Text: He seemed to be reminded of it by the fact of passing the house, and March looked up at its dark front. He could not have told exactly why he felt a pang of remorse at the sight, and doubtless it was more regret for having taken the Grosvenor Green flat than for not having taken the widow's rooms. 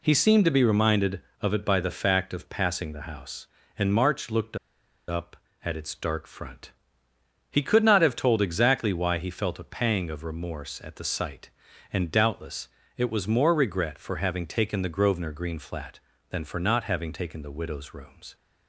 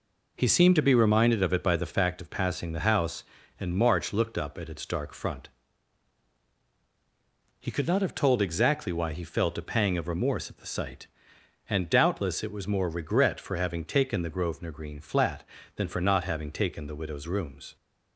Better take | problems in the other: second | pauses between "looked" and "up"; noticeable; at 4.5 s; 0.51 s long // pauses between "doubtless" and "it"; slight; at 12.6 s; 0.30 s long

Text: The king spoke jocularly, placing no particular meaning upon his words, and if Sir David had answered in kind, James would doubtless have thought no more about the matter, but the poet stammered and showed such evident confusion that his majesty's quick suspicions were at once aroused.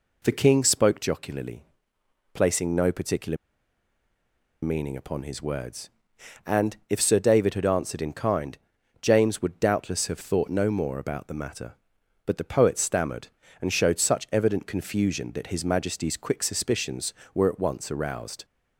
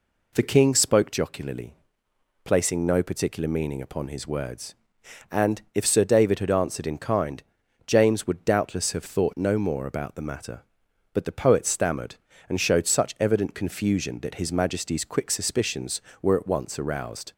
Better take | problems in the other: second | pauses between "particular" and "meaning"; strong; at 3.3 s; 1.2 s long

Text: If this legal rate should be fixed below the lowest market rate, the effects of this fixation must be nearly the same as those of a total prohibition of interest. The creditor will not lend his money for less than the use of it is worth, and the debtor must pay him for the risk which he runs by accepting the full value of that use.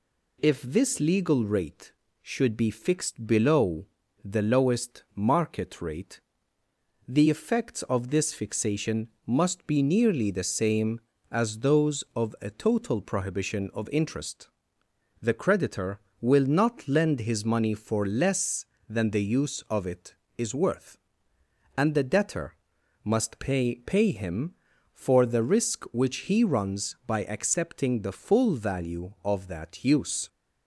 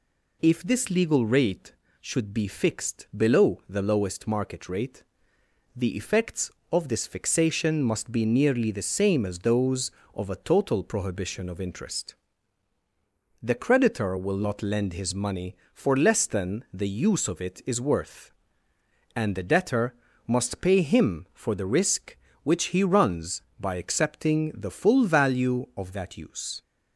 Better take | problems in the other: second | pauses between "below" and "the"; slight; at 3.8 s; 0.36 s long // pauses between "fixation" and "must"; slight; at 9.0 s; 0.18 s long // pauses between "debtor" and "must"; noticeable; at 22.5 s; 0.50 s long; slight in the second // says "pay" twice; at 23.8 s

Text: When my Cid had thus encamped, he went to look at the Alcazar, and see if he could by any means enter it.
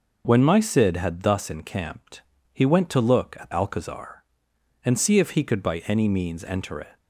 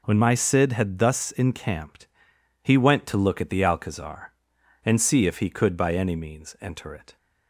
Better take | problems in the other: second | skips "the"; at 3.5 s

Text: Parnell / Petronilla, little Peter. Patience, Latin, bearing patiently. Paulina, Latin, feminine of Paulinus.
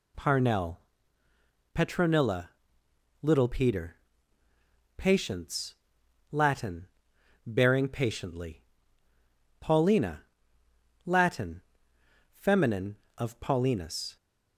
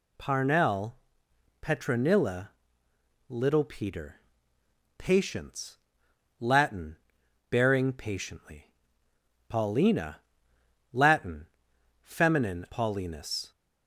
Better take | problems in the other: first | skips "of"; at 12.6 s

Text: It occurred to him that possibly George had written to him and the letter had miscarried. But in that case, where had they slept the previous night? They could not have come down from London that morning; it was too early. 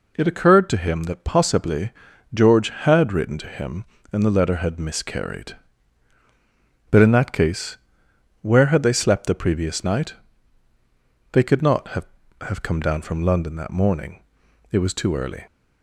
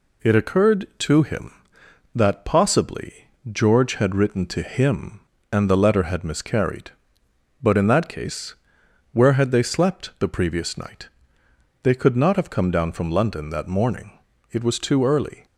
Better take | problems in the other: second | pauses between "possibly" and "George"; at 1.9 s; 0.42 s long; slight in the second // says "have" twice; at 12.4 s

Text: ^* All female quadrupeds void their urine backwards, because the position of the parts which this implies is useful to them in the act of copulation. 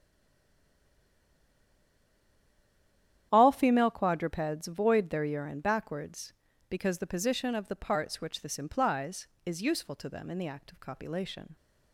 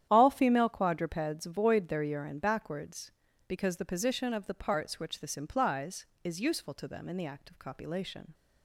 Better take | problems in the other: second | stays silent before the first word; strong; until 3.3 s; 3.3 s long // starts louder than the rest; strong; until 4.3 s; 10.5 dB; strong in the second

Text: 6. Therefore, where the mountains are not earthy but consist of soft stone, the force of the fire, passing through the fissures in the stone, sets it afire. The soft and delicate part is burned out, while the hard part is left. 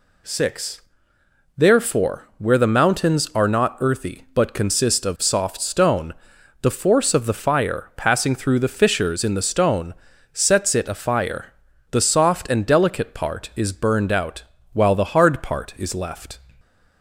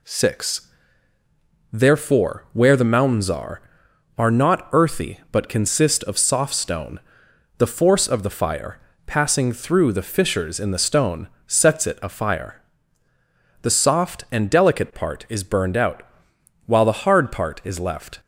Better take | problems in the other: first | says "are" twice; at 4.1 s

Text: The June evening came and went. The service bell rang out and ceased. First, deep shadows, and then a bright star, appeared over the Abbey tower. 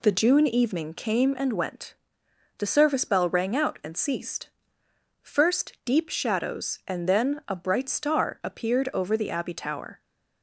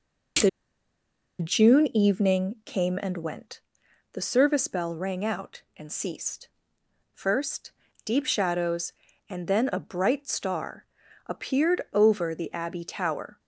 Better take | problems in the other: first | pauses between "The" and "June"; noticeable; at 0.4 s; 0.91 s long

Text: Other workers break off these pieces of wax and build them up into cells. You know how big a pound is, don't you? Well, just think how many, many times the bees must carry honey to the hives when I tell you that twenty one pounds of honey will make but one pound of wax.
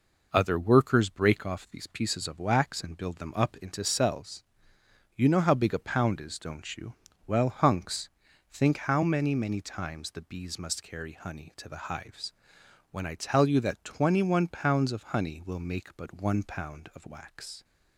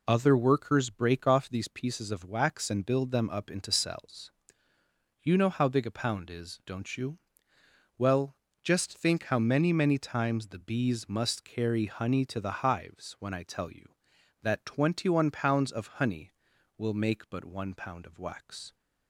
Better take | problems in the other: second | says "hunks" for "just"; at 7.4 s // pauses between "hives" and "when"; noticeable; at 12.3 s; 0.58 s long

